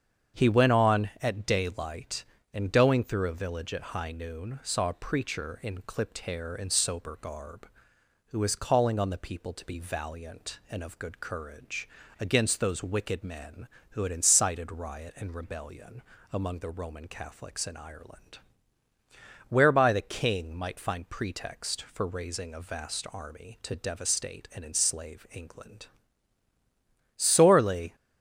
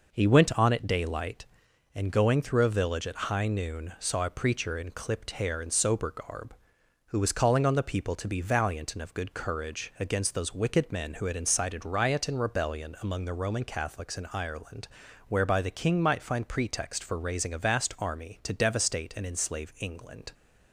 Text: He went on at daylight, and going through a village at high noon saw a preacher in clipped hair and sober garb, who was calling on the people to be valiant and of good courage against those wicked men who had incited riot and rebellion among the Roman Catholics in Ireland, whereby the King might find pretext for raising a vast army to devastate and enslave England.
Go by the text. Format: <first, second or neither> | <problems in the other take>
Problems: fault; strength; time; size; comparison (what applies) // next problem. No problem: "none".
second | starts louder than the rest; strong; until 1.4 s; 7.5 dB // pauses between "courage" and "against"; slight; at 11.8 s; 0.32 s long // pauses between "rebellion" and "among"; slight; at 16.0 s; 0.32 s long // goes on to say "Sorely"; noticeable; from 27.1 s on; 0.80 s long